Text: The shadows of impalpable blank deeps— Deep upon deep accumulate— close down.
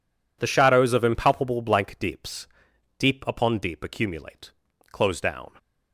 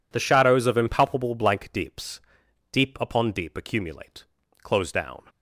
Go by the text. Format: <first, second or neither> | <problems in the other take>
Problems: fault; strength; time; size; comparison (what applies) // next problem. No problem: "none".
neither | none